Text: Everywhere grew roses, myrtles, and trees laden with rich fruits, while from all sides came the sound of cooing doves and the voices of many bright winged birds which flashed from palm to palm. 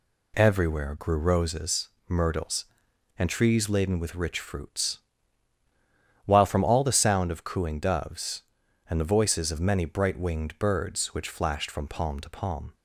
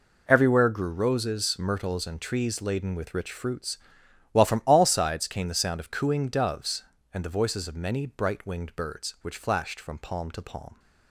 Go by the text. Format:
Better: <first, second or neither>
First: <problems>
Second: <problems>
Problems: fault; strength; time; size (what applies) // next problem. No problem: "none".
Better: second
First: skips "sides came"; at 6.8 s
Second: none